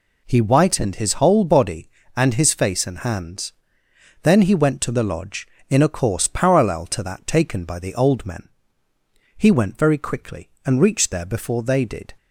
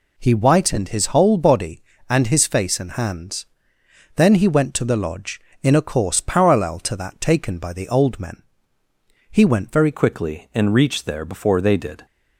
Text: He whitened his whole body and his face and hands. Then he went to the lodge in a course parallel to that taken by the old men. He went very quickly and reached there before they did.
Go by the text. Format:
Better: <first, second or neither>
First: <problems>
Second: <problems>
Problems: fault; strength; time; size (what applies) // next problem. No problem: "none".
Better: first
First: none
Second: changes voice at "quickly"; from 9.9 s on; 2.1 s long